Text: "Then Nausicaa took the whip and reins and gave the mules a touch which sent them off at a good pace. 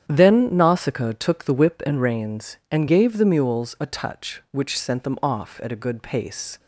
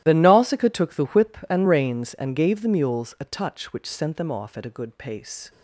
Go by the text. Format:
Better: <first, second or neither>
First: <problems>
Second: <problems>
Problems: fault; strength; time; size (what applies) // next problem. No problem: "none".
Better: first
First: starts louder than the rest; strong; until 1.0 s; 9.5 dB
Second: gets quieter; strong; throughout; 17.5 dB // starts louder than the rest; strong; until 1.0 s; 14 dB